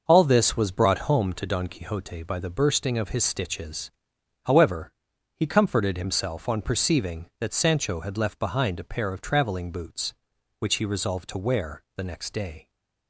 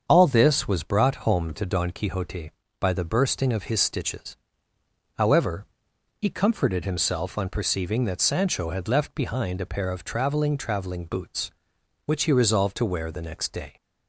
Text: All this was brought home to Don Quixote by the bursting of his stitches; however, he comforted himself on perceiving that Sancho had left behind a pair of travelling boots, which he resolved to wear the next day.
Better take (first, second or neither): first